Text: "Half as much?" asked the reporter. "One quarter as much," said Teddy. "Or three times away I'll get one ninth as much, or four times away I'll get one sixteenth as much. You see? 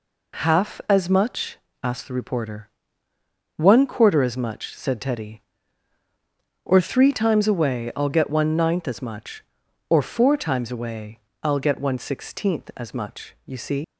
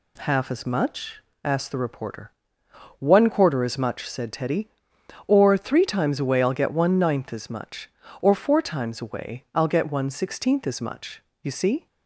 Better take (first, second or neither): second